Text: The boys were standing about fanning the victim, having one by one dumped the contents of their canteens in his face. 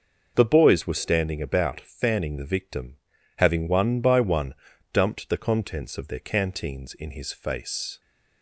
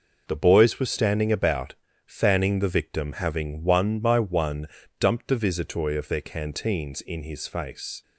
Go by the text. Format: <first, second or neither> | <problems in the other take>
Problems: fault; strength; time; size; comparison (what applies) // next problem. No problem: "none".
first | pauses between "about" and "fanning"; slight; at 1.7 s; 0.30 s long // pauses between "one" and "dumped"; slight; at 4.6 s; 0.32 s long; also in the first // says "visitoi" for "contents"; at 5.3 s